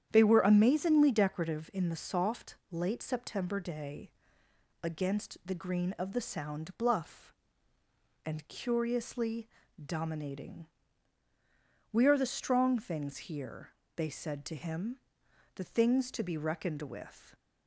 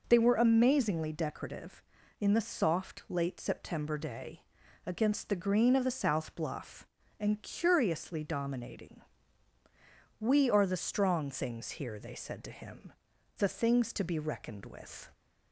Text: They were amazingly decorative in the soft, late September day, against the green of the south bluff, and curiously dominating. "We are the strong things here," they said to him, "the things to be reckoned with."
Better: second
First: starts louder than the rest; strong; until 1.1 s; 9.5 dB // says "sound" for "south"; at 6.2 s // pauses between "curiously" and "dominating"; slight; at 9.4 s; 0.36 s long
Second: none

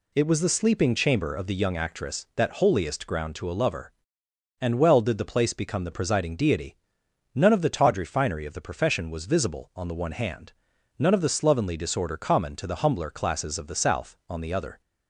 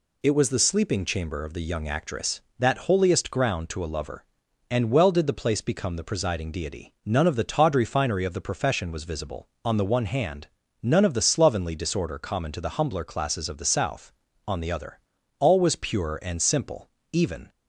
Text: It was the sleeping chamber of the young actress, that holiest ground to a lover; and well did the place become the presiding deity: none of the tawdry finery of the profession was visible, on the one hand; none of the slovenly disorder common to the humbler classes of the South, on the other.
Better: first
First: none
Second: goes on to say "All was pure and simple even"; strong; from 15.3 s on; 2.1 s long

